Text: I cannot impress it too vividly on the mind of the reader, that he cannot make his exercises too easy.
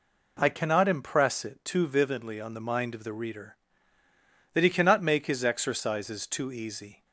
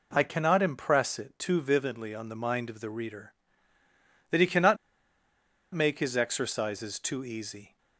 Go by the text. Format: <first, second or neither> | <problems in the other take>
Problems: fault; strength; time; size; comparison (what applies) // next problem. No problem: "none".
first | pauses between "cannot" and "make"; noticeable; at 4.7 s; 0.96 s long